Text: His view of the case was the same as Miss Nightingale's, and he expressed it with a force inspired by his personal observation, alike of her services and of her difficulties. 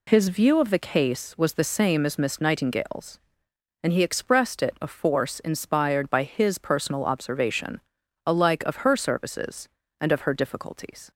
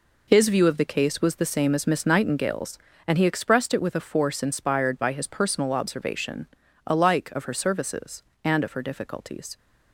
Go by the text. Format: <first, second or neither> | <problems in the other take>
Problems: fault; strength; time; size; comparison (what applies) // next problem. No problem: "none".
second | skips "with"; at 4.7 s